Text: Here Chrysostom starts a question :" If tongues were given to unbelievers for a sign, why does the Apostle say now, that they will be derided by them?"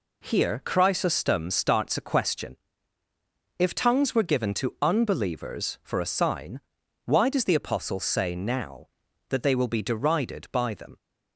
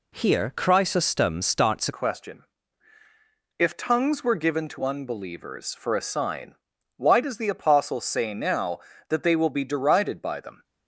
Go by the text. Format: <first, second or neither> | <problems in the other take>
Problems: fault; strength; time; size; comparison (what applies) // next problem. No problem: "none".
first | changes voice at "question"; from 1.9 s on; 8.7 s long